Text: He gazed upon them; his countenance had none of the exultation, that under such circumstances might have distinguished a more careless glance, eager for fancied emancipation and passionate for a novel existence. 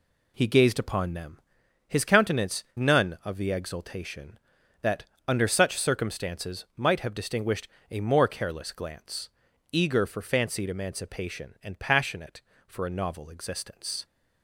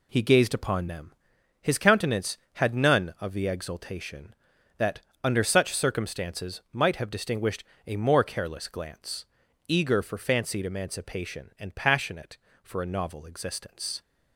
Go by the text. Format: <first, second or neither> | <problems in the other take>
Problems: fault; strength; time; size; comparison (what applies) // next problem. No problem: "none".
second | skips "had"; at 2.7 s // pauses between "that" and "under"; slight; at 5.0 s; 0.22 s long; slight in the second // pauses between "distinguished" and "a"; slight; at 7.6 s; 0.22 s long; slight in the second